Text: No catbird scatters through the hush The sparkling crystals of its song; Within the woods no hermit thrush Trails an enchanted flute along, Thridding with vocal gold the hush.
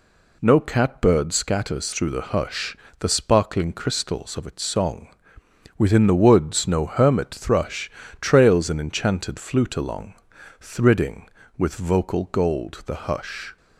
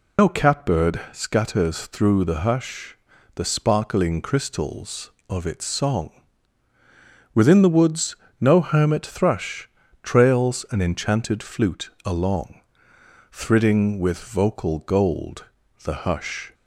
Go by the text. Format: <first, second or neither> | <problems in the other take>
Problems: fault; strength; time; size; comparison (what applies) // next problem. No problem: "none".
first | loses the start of "No"; at 0.1 s; 100 ms // pauses between "hush" and "The"; at 2.9 s; 0.40 s long; slight in the first // pauses between "woods" and "no"; slight; at 8.1 s; 0.24 s long // pauses between "thrush" and "Trails"; slight; at 9.6 s; 0.34 s long; slight in the first // pauses between "flute" and "along"; slight; at 11.8 s; 0.16 s long // pauses between "gold" and "the"; at 15.4 s; 0.40 s long